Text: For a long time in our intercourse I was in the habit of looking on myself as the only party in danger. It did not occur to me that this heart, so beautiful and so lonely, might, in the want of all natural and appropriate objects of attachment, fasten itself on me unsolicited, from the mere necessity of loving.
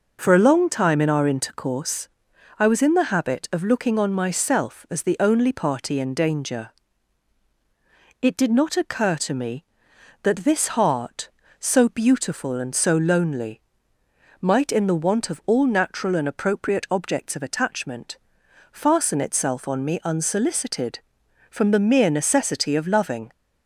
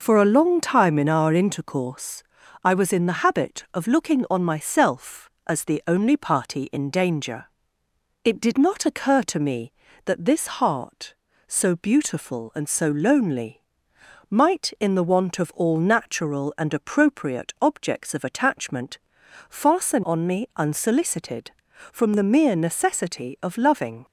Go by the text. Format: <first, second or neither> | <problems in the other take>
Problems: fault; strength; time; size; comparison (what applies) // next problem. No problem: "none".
first | pauses between "intercourse" and "I"; at 2.2 s; 0.40 s long; noticeable in the first // skips "itself"; at 20.0 s